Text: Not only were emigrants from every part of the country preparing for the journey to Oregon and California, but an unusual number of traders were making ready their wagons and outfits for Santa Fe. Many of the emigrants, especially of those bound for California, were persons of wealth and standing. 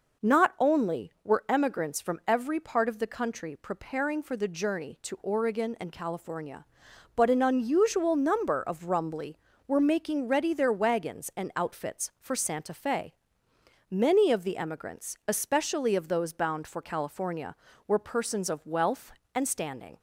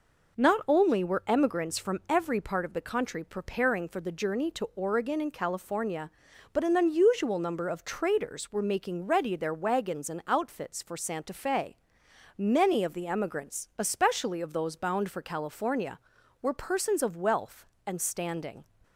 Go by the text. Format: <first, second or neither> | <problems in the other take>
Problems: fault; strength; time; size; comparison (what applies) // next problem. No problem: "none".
second | says "rumbly" for "traders"; at 8.8 s